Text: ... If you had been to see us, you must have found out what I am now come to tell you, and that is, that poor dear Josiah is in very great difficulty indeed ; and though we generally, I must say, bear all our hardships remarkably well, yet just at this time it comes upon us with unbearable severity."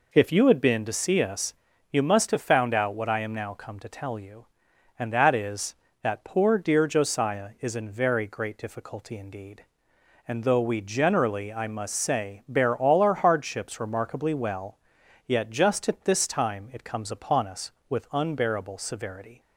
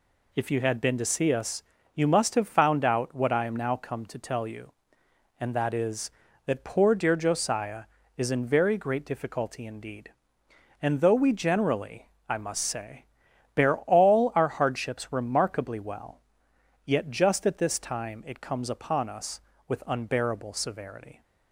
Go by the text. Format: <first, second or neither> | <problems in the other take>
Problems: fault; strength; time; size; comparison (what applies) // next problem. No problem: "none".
neither | none